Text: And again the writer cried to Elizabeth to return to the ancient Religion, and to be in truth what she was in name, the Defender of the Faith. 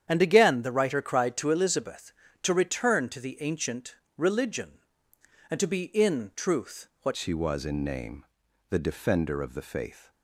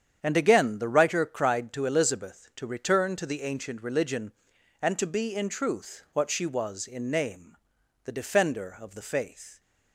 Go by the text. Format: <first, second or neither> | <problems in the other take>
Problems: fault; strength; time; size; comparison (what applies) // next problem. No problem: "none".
second | starts louder than the rest; strong; until 1.0 s; 9 dB; strong in the second // pauses between "ancient" and "Religion"; slight; at 3.9 s; 0.24 s long // pauses between "truth" and "what"; slight; at 6.8 s; 0.16 s long // changes voice at "she"; from 7.1 s on; 3.0 s long